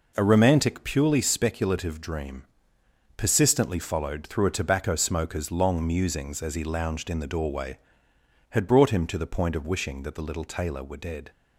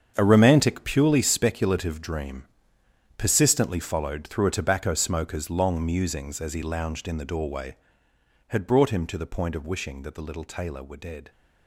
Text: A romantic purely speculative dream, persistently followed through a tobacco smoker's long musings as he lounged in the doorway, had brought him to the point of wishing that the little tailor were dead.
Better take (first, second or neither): first